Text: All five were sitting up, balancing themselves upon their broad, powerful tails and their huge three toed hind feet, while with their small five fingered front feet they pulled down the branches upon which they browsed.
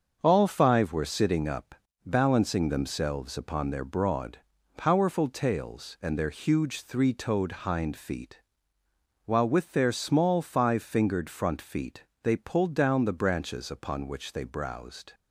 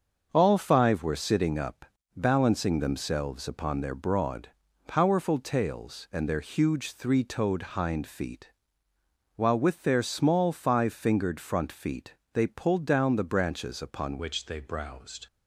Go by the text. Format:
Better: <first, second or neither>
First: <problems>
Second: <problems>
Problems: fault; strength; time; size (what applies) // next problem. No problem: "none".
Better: first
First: starts louder than the rest; until 1.2 s; 6.5 dB // pauses between "feet" and "they"; slight; at 12.0 s; 0.20 s long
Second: starts louder than the rest; until 1.3 s; 6.5 dB // pauses between "feet" and "they"; slight; at 12.1 s; 0.20 s long // changes voice at "which"; from 14.1 s on; 1.1 s long